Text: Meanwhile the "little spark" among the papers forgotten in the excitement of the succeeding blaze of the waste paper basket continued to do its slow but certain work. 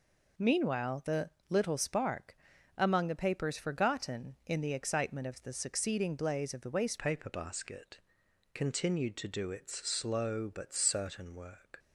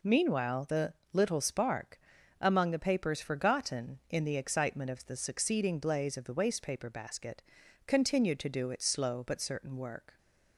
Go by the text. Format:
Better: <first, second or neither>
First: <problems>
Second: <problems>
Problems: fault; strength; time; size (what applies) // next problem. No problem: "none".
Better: second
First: pauses between "the" and "little"; slight; at 1.2 s; 0.20 s long // pauses between "spark" and "among"; at 2.3 s; 0.40 s long // changes voice at "paper"; from 6.9 s on; 4.8 s long // pauses between "basket" and "continued"; noticeable; at 7.9 s; 0.54 s long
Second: pauses between "the" and "little"; slight; at 0.9 s; 0.20 s long // pauses between "spark" and "among"; at 1.9 s; 0.40 s long // pauses between "basket" and "continued"; noticeable; at 7.4 s; 0.46 s long